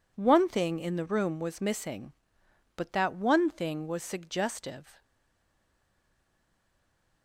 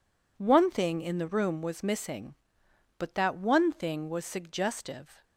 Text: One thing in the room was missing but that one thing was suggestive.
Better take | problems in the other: second | stays silent after the last word; from 5.0 s on; 2.2 s long

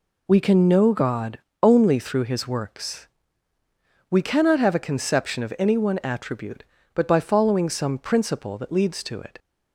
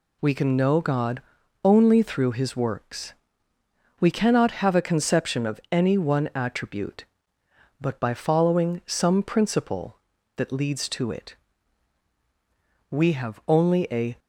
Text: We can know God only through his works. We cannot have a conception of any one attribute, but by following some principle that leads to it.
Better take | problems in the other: first | pauses between "God" and "only"; at 1.2 s; 0.42 s long; slight in the first // goes on to say "We have only a"; noticeable; from 12.9 s on; 1.2 s long

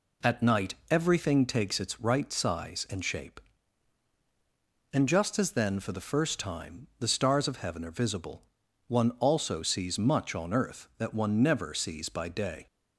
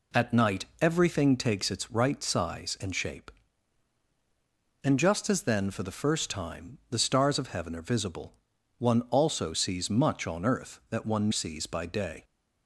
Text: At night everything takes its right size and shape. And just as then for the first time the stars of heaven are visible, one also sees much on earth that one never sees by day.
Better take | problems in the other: first | skips "never"; at 11.3 s

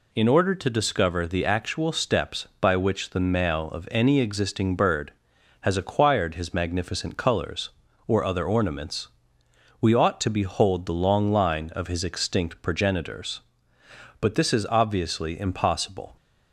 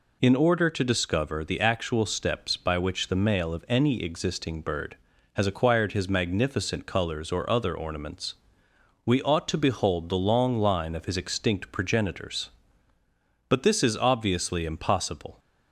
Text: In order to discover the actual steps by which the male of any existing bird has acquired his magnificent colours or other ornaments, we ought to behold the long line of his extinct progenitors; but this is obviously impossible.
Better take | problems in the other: neither | none

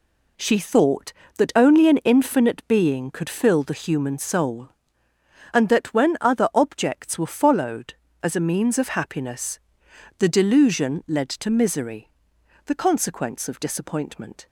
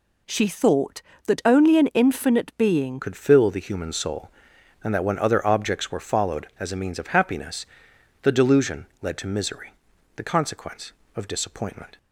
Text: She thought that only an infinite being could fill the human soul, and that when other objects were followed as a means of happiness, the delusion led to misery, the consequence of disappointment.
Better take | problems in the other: first | changes voice at "could"; from 3.0 s on; 8.9 s long // pauses between "delusion" and "led"; slight; at 8.8 s; 0.16 s long

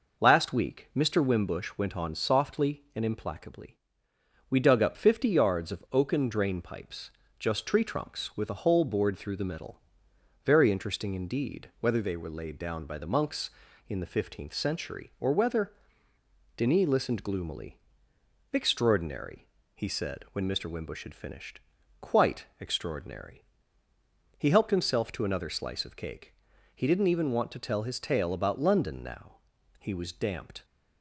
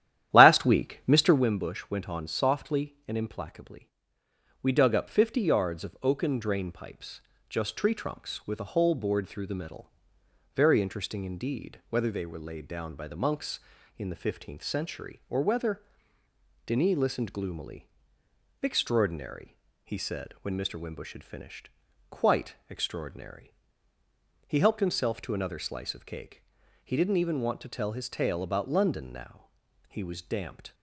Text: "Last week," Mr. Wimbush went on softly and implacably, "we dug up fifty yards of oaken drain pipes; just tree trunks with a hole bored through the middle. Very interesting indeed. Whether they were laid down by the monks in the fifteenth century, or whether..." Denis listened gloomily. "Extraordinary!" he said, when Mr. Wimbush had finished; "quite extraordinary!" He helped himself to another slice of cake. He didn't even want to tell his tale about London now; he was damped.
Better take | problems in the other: first | starts louder than the rest; strong; until 1.5 s; 11.5 dB

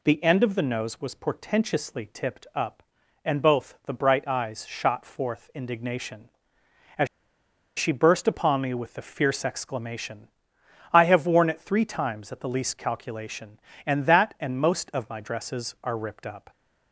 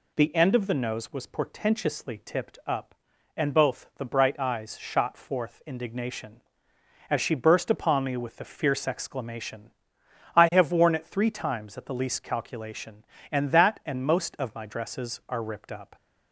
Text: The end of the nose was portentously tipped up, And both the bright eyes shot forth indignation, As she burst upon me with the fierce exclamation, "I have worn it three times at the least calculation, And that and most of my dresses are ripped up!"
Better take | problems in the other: second | pauses between "As" and "she"; noticeable; at 7.0 s; 0.70 s long

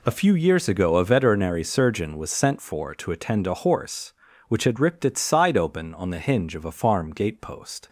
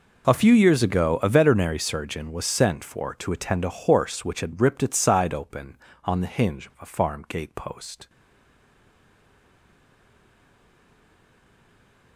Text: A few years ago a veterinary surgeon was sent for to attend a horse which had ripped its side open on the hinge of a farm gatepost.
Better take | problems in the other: first | stays silent after the last word; strong; from 8.0 s on; 4.1 s long

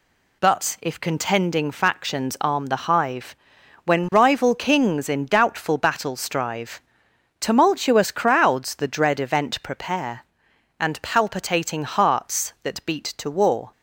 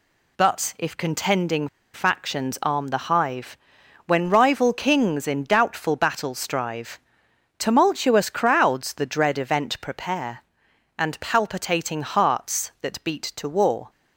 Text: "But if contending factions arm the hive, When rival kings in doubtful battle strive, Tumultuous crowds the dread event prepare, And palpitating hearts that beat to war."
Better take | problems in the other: first | pauses between "contending" and "factions"; slight; at 1.6 s; 0.26 s long

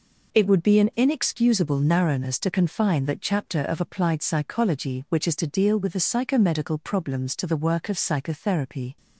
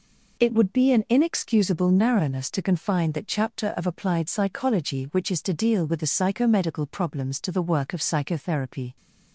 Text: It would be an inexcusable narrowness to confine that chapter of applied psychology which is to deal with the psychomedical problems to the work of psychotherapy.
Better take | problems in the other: neither | none

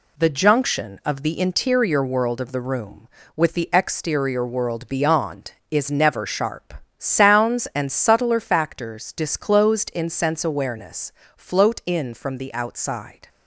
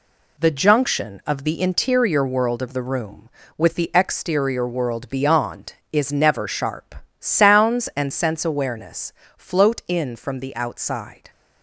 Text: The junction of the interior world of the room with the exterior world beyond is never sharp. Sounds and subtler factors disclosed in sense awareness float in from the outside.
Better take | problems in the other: first | skips "subtler factors disclosed in"; at 8.1 s // pauses between "awareness" and "float"; slight; at 9.1 s; 0.24 s long; slight in the first

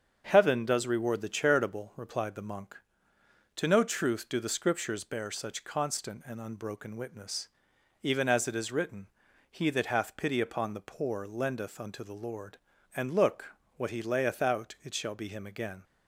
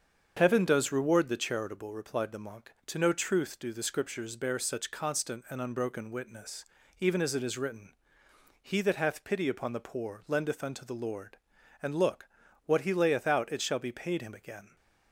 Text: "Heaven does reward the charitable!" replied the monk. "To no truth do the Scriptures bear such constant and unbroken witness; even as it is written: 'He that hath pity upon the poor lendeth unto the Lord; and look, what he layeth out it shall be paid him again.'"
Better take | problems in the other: second | starts louder than the rest; until 1.3 s; 7 dB; strong in the second // skips "paid"; at 15.2 s

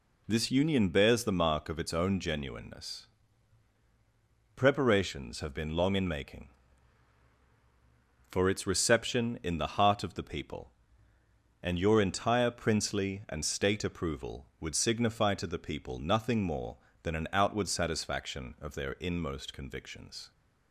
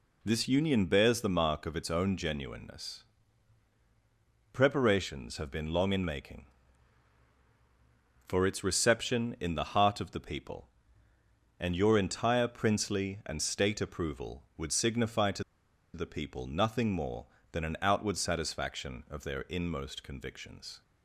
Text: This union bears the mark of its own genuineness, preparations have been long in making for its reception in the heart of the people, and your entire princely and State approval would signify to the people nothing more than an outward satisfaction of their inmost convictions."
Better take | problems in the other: first | pauses between "to" and "the"; noticeable; at 15.4 s; 0.51 s long

